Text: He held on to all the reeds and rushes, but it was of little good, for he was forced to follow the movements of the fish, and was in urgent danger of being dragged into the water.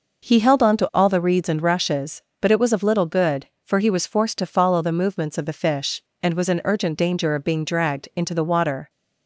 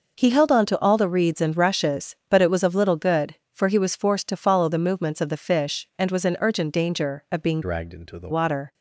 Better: first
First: none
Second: changes voice from "dragged" to "the"; from 7.6 to 8.2 s; 0.6 s long

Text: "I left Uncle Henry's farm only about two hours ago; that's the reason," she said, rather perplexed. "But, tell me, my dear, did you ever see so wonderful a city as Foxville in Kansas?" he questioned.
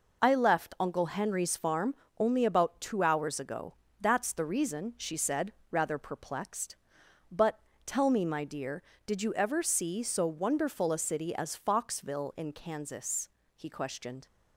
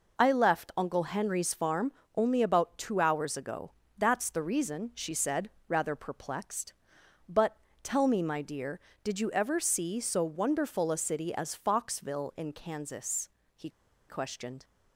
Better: first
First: pauses between "farm" and "only"; slight; at 1.9 s; 0.22 s long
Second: pauses between "farm" and "only"; slight; at 1.9 s; 0.22 s long // pauses between "he" and "questioned"; at 13.6 s; 0.40 s long

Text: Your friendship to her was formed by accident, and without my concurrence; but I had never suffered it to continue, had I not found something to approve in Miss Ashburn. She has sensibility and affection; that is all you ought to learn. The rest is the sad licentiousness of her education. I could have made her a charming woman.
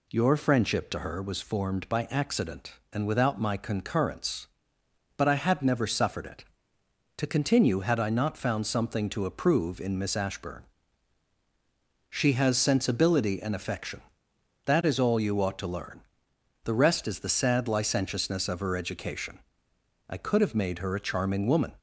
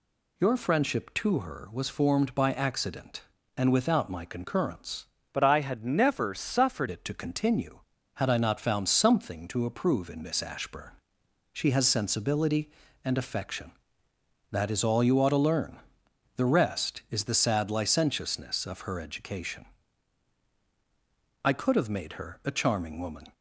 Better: first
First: none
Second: changes voice from "but" to "suffered"; from 5.3 to 6.8 s; 1.5 s long

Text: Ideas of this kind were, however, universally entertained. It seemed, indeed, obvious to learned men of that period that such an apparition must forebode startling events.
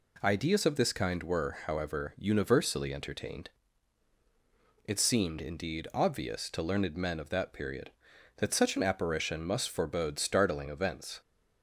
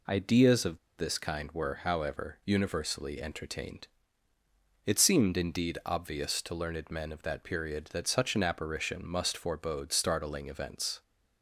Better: first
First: none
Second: pauses between "of" and "this"; slight; at 0.7 s; 0.19 s long

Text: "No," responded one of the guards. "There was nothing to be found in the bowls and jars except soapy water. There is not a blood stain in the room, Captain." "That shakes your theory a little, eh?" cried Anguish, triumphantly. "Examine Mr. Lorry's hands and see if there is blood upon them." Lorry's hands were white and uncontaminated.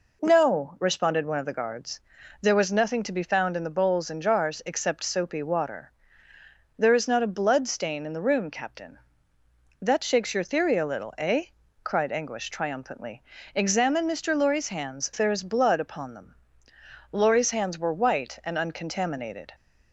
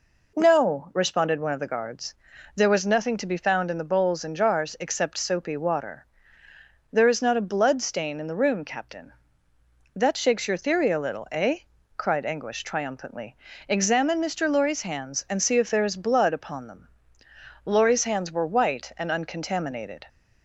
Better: second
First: skips "and see if"; at 15.1 s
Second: none

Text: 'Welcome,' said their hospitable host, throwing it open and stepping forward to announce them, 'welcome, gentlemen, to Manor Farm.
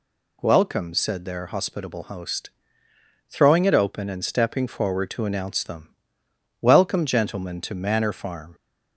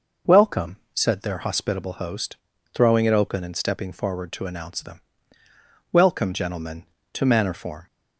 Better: first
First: none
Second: says "Form" for "Farm"; at 7.5 s

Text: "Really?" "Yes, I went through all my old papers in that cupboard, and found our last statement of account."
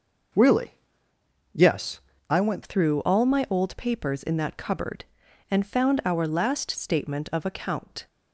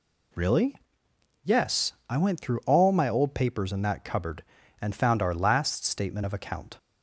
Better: second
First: changes voice at "through"; from 2.6 s on; 5.4 s long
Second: none

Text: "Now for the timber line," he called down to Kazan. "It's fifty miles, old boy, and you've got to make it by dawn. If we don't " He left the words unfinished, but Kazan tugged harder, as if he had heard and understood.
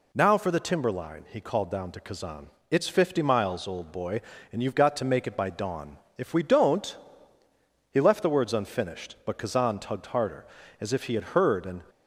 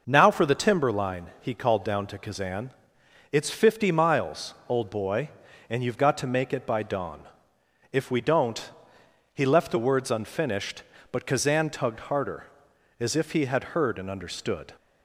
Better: second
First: stops before "understood"; at 11.8 s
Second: none

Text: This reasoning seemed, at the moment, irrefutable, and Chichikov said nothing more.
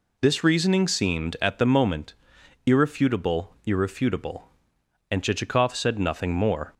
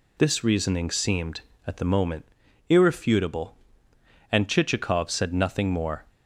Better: second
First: says "irrefutable" twice; at 3.6 s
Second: none

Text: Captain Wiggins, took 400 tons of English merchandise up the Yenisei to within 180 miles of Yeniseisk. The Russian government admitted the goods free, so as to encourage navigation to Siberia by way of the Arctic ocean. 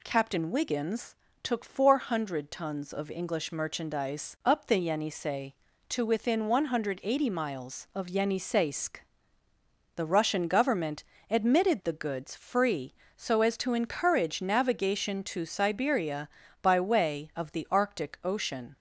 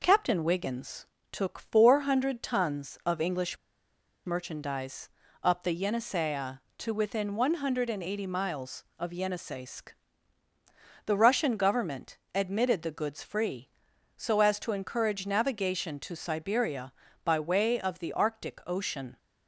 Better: first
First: pauses between "government" and "admitted"; slight; at 11.0 s; 0.26 s long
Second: pauses between "English" and "merchandise"; noticeable; at 3.5 s; 0.69 s long // pauses between "merchandise" and "up"; slight; at 5.0 s; 0.34 s long // pauses between "government" and "admitted"; slight; at 12.1 s; 0.18 s long

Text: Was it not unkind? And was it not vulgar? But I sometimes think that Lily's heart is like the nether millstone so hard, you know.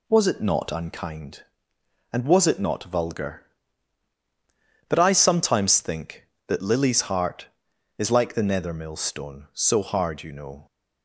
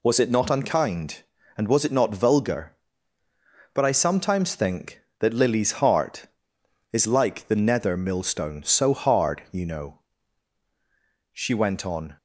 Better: first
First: none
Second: goes on to say "She went on"; noticeable; from 11.3 s on; 0.86 s long

